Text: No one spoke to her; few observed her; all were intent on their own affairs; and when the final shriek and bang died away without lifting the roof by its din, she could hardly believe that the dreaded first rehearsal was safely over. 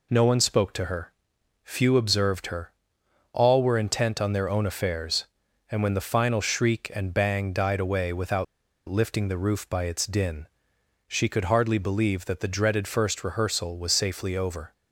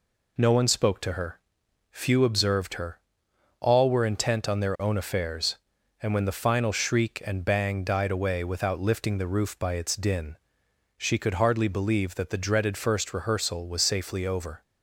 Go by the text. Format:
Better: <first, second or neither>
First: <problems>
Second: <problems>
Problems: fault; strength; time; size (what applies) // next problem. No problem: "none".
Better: second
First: pauses between "without" and "lifting"; at 8.4 s; 0.43 s long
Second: none